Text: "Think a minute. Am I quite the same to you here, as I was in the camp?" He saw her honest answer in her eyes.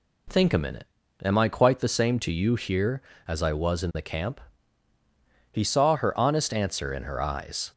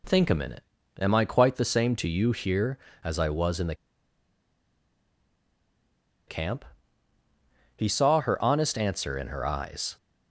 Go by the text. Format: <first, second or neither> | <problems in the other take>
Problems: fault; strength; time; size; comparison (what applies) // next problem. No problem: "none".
first | pauses between "the" and "camp"; strong; at 3.7 s; 2.5 s long